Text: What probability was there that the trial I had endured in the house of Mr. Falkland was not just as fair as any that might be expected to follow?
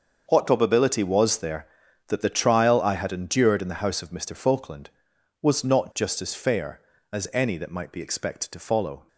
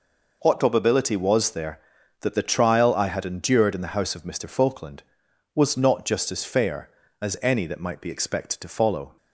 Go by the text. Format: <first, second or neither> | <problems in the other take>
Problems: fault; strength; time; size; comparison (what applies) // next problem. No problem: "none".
second | gets quieter; strong; throughout; 13 dB